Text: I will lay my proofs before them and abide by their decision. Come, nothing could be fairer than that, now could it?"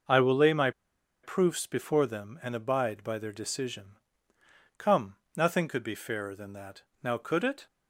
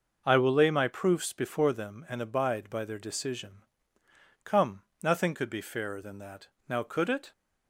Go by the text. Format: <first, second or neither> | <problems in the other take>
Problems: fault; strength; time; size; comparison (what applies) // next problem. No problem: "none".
second | pauses between "my" and "proofs"; noticeable; at 0.7 s; 0.53 s long